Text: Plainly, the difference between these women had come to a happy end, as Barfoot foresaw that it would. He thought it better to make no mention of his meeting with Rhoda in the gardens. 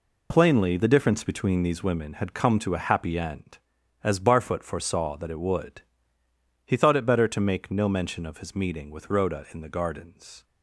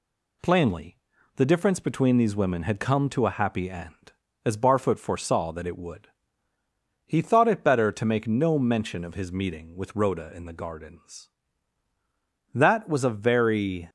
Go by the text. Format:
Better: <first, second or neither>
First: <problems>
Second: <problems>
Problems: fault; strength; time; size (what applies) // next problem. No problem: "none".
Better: first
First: none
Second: goes on to say "That was a very"; from 12.5 s on; 1.3 s long